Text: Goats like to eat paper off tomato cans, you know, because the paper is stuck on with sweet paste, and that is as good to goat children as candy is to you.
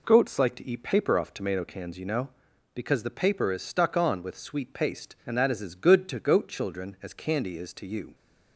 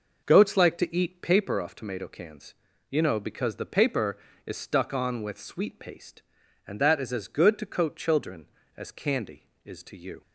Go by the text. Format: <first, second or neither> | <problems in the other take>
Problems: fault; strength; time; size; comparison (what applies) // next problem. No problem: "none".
first | says "coat" for "goat"; at 7.6 s